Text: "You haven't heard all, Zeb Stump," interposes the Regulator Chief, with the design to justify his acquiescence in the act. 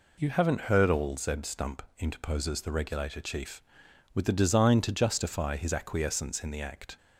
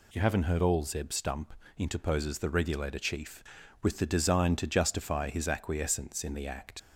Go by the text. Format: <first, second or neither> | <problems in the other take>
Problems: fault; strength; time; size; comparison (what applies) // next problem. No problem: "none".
first | leaves "act" unfinished; at 6.7 s; 40 ms